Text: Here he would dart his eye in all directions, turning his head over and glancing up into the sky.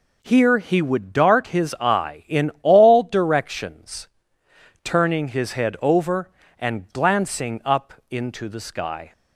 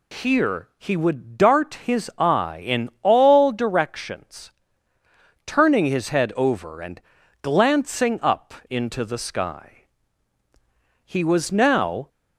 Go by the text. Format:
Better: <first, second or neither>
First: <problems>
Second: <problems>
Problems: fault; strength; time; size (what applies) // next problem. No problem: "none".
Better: first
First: pauses between "up" and "into"; slight; at 7.9 s; 0.16 s long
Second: pauses between "and" and "glancing"; at 7.0 s; 0.40 s long // pauses between "up" and "into"; slight; at 8.5 s; 0.16 s long // goes on to say "He was now"; noticeable; from 11.0 s on; 1.0 s long